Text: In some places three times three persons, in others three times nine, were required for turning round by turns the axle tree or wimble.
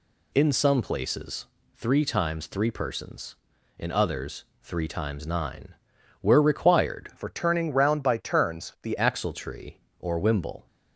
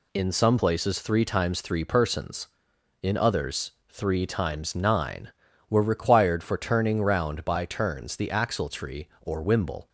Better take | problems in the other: second | pauses between "places" and "three"; slight; at 1.4 s; 0.32 s long // pauses between "others" and "three"; slight; at 4.4 s; 0.18 s long; slight in the second // changes voice from "for" to "the"; from 7.1 to 8.9 s; 1.8 s long

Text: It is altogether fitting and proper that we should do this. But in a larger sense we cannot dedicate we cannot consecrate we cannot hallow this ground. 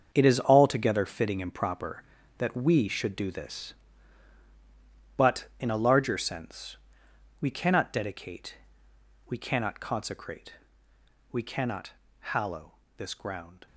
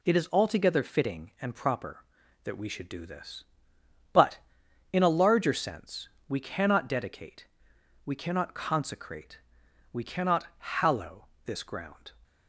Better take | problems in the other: second | gets quieter; strong; throughout; 11 dB // pauses between "sense" and "we"; noticeable; at 6.7 s; 0.66 s long; slight in the second // pauses between "dedicate" and "we"; noticeable; at 8.5 s; 0.72 s long; noticeable in the second // pauses between "consecrate" and "we"; noticeable; at 10.5 s; 0.76 s long; noticeable in the second // pauses between "cannot" and "hallow"; slight; at 11.9 s; 0.28 s long // pauses between "hallow" and "this"; slight; at 12.7 s; 0.24 s long; slight in the second

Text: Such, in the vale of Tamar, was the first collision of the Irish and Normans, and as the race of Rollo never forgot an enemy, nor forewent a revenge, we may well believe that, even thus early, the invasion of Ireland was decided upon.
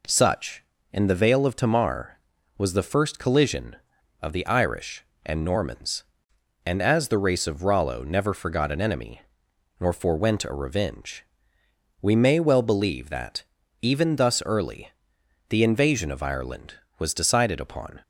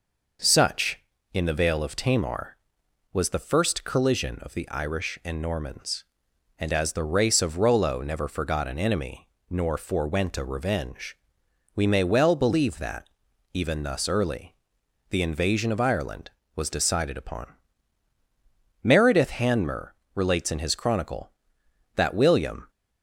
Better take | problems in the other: first | goes on to say "Meredith Hanmer relates in his Chronicle that William"; strong; from 18.8 s on; 3.8 s long

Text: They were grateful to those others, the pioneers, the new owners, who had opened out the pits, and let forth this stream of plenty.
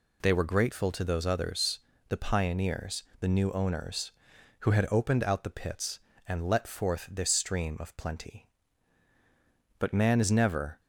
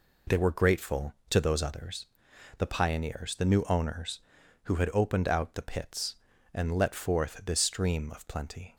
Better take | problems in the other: second | goes on to say "But man is never"; noticeable; from 9.7 s on; 1.0 s long

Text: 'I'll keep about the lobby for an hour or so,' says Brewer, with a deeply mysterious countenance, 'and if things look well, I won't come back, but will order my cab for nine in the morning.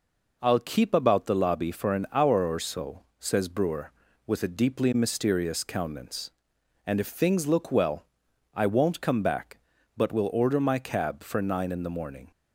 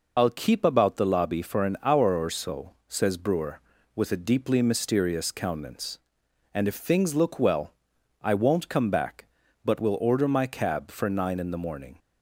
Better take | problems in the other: first | loses the start of "I'll"; at 0.1 s; 65 ms

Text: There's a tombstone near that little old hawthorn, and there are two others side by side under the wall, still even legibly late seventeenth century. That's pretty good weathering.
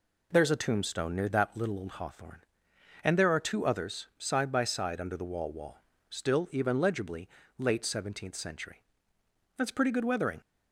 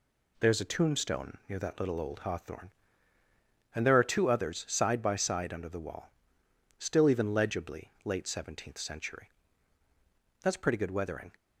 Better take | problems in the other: second | says "wall" twice; at 5.5 s // pauses between "legibly" and "late"; slight; at 7.2 s; 0.30 s long

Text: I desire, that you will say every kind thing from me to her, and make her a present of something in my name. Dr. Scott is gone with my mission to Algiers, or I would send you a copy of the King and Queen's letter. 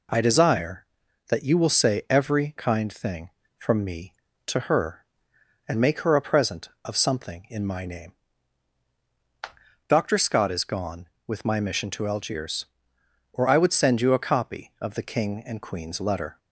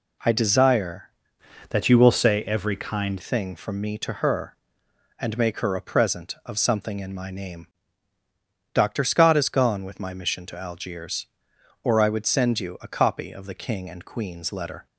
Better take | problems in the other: first | changes voice from "that" to "kind"; from 1.7 to 3.1 s; 1.4 s long

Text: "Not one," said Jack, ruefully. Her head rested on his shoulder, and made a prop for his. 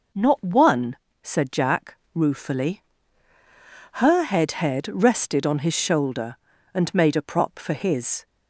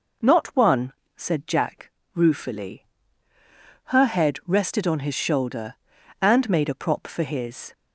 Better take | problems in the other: second | says "head" twice; at 4.5 s

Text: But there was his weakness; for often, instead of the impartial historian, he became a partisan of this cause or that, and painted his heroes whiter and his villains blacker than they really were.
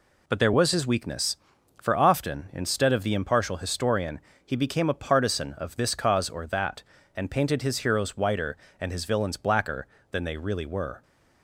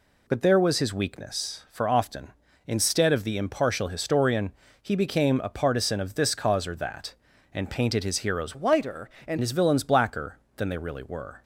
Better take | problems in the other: first | changes voice from "whiter" to "and"; from 8.5 to 9.3 s; 0.8 s long

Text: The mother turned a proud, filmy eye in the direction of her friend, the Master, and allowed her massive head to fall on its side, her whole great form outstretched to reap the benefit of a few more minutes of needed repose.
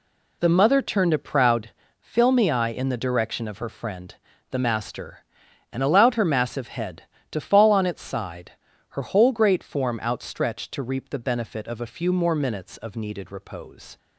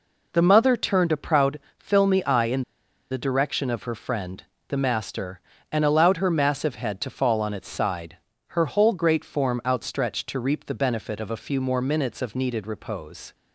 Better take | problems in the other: first | pauses between "in" and "the"; noticeable; at 2.6 s; 0.49 s long

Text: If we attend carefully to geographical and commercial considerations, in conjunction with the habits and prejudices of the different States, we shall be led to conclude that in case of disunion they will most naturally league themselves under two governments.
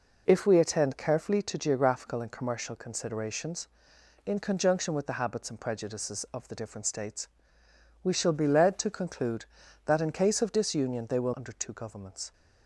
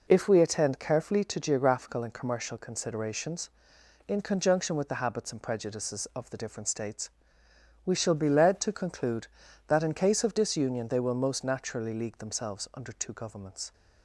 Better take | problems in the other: second | skips "most naturally league themselves"; at 11.3 s

